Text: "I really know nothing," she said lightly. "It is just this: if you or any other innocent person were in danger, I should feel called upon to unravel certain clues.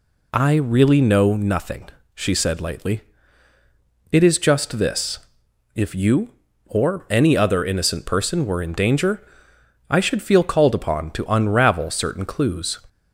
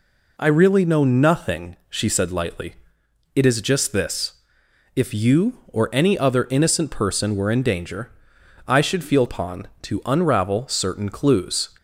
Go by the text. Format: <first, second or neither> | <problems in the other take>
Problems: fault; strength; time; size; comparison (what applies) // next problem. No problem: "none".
first | skips "called"; at 9.2 s